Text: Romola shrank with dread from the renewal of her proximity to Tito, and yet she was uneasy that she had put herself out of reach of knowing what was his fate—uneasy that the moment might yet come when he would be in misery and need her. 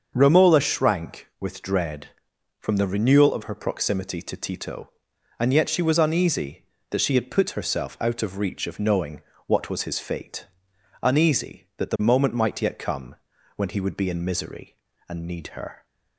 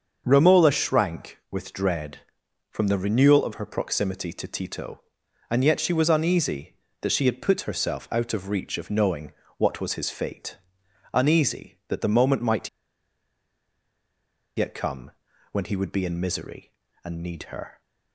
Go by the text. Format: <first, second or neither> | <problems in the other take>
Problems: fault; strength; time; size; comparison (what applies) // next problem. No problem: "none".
first | starts louder than the rest; until 1.2 s; 6.5 dB; also in the first // pauses between "knowing" and "what"; slight; at 9.3 s; 0.26 s long; slight in the first // pauses between "might" and "yet"; strong; at 12.6 s; 1.8 s long // pauses between "come" and "when"; at 15.1 s; 0.42 s long; also in the first